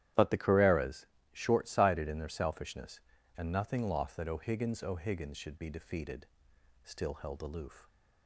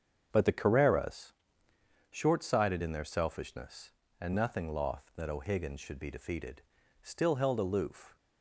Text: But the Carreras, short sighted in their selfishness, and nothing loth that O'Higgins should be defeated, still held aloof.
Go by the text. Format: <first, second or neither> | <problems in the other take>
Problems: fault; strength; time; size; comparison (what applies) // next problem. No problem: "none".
second | starts louder than the rest; strong; until 1.4 s; 12 dB; strong in the second // says "O'Higgins" twice; at 4.8 s